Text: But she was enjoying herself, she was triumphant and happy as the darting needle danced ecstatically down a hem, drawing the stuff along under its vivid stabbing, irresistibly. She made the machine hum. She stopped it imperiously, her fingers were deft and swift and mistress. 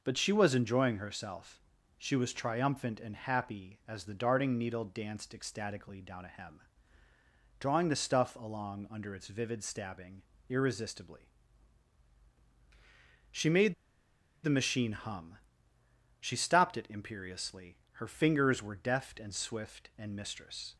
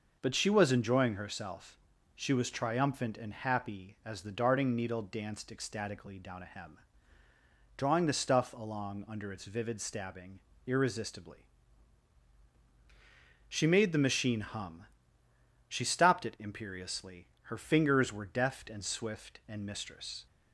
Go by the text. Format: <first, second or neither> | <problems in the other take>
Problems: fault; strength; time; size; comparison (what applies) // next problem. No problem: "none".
second | pauses between "made" and "the"; noticeable; at 13.7 s; 0.69 s long